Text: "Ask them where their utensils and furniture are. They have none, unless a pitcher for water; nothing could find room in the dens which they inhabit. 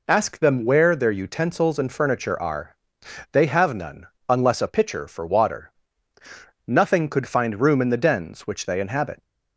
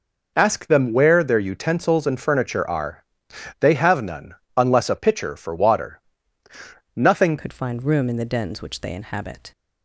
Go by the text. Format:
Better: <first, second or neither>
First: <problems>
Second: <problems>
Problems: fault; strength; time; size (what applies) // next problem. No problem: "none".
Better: first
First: none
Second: changes voice at "could"; from 7.3 s on; 2.2 s long